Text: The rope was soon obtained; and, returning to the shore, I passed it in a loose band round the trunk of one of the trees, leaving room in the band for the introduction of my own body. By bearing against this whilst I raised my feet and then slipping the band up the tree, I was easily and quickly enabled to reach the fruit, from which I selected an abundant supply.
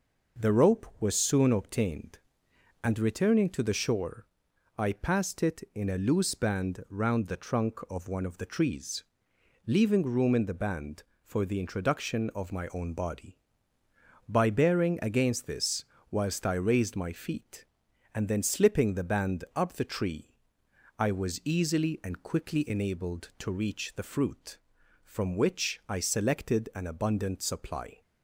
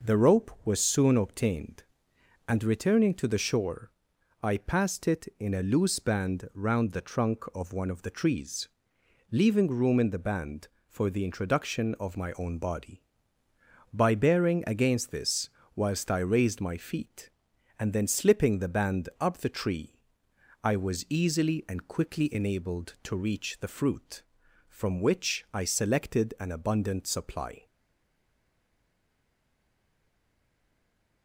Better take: first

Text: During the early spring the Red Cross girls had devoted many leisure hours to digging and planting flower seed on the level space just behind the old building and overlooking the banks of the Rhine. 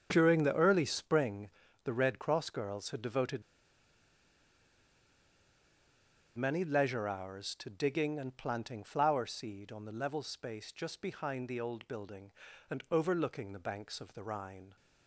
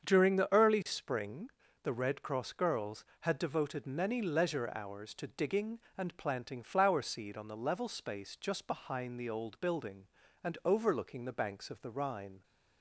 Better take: second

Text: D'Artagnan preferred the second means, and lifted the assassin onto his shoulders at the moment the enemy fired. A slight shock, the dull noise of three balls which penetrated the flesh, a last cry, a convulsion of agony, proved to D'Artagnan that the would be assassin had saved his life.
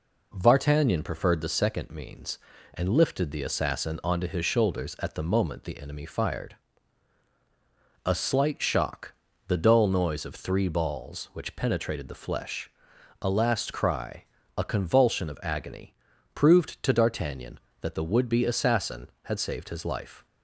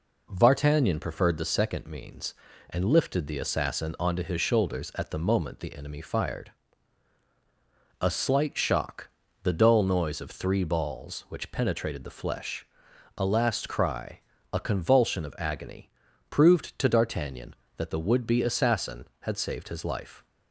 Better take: neither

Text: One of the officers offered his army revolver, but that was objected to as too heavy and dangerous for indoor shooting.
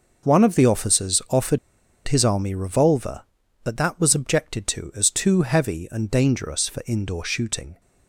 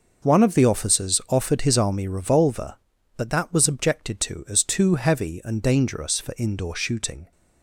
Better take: second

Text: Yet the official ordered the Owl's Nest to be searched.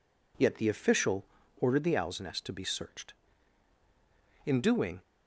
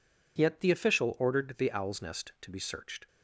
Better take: second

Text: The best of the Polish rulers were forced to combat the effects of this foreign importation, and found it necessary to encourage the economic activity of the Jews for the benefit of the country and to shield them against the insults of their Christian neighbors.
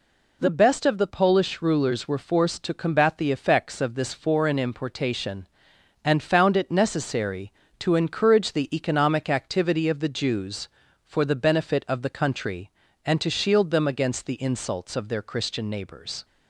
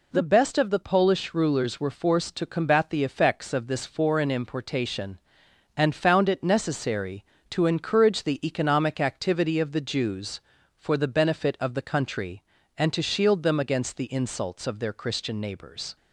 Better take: neither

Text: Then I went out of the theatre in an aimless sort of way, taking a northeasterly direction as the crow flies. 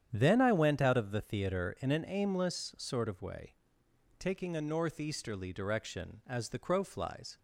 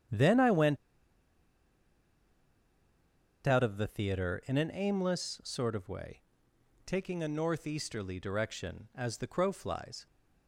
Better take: first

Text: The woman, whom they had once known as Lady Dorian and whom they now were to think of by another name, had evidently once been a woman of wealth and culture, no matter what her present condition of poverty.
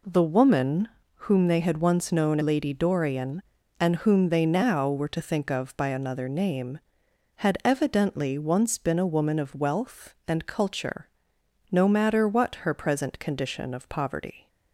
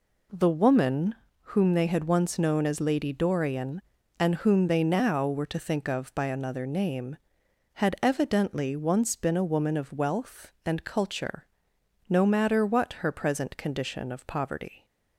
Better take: second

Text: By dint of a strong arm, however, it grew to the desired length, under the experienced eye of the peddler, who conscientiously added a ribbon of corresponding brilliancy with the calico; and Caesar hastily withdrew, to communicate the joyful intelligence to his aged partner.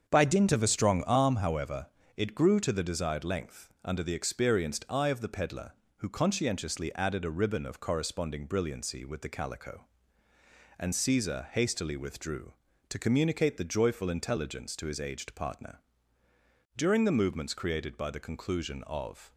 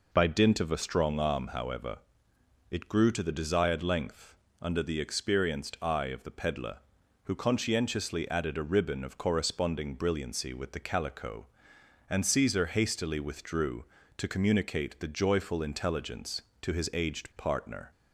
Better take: second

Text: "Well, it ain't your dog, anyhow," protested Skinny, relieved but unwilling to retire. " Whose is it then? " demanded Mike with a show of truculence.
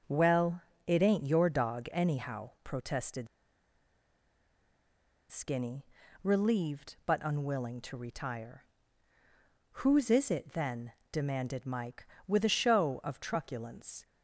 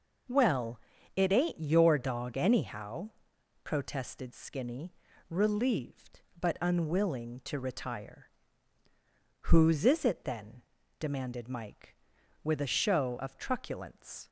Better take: second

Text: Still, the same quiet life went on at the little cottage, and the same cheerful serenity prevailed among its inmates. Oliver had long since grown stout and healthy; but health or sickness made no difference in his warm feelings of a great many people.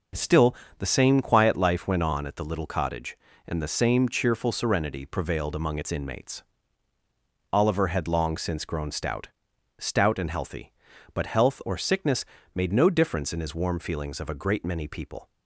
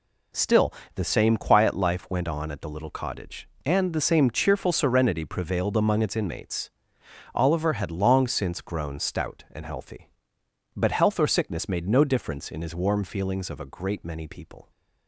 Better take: second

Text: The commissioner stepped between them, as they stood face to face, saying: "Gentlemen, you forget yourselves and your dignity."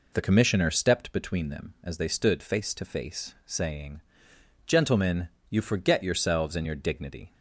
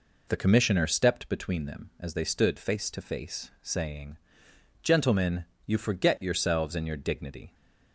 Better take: neither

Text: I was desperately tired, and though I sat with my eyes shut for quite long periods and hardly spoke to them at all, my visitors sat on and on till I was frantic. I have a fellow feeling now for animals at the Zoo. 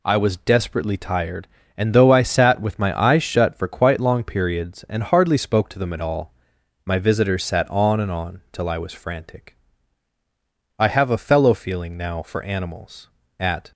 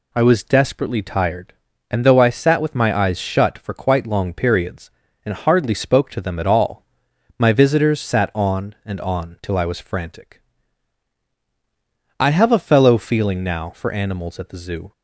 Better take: second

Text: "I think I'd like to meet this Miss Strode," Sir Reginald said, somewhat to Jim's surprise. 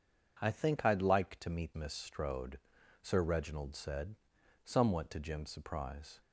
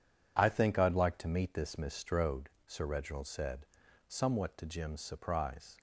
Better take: second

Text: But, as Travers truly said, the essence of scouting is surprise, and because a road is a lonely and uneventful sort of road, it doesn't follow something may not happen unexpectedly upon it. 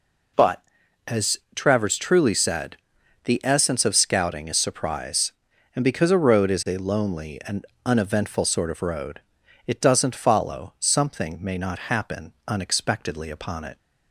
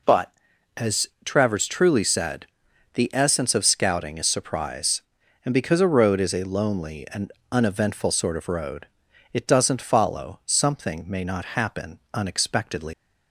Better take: first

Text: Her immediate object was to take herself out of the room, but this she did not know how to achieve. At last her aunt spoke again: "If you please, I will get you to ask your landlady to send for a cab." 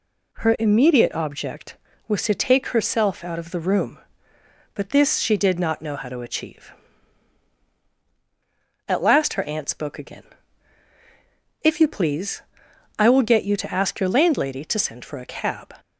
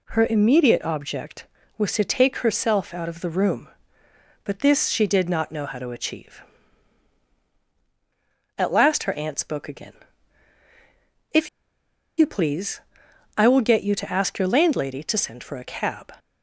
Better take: first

